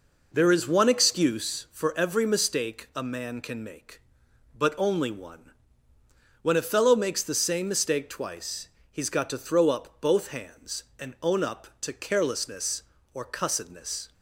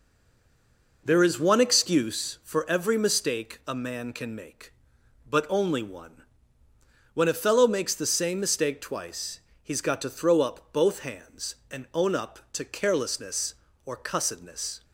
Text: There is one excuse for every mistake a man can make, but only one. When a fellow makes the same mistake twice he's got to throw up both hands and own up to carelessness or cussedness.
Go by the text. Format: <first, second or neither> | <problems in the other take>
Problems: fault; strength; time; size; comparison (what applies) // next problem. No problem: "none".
first | stays silent before the first word; until 1.0 s; 1.0 s long // pauses between "twice" and "he's"; slight; at 9.4 s; 0.22 s long; slight in the first